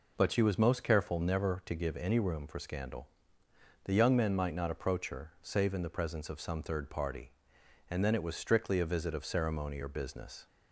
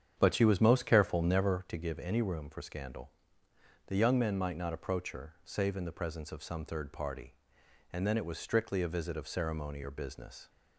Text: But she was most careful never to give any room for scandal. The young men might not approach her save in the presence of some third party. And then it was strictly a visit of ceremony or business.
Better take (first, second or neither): first